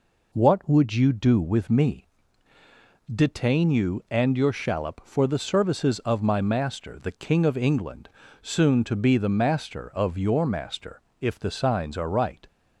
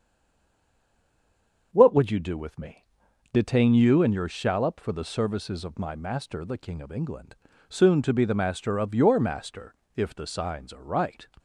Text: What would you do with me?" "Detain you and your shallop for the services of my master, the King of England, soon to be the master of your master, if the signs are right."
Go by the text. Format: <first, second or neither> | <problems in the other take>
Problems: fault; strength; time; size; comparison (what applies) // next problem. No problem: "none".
first | stays silent before the first word; noticeable; until 1.7 s; 1.7 s long // starts louder than the rest; until 2.7 s; 6.5 dB